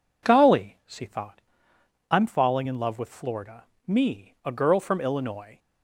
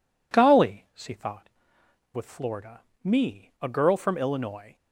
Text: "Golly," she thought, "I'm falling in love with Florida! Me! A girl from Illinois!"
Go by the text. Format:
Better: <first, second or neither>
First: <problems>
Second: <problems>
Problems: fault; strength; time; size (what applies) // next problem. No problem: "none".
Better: first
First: none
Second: skips "I'm falling in love"; at 1.8 s